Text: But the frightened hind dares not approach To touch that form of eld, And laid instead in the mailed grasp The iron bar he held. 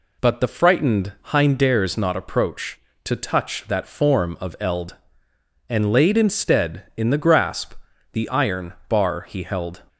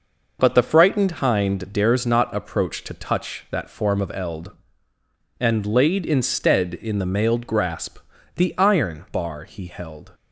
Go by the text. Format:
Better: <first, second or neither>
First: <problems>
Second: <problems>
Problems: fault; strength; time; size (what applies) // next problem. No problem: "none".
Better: second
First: skips "mailed"; at 7.1 s // pauses between "grasp" and "The"; at 7.7 s; 0.38 s long // pauses between "iron" and "bar"; slight; at 8.7 s; 0.16 s long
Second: pauses between "grasp" and "The"; at 7.9 s; 0.38 s long